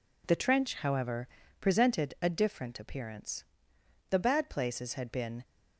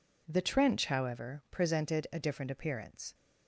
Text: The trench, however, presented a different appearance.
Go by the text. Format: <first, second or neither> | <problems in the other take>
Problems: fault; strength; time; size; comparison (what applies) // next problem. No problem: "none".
second | goes on to say "The bad places had been"; from 4.0 s on; 1.3 s long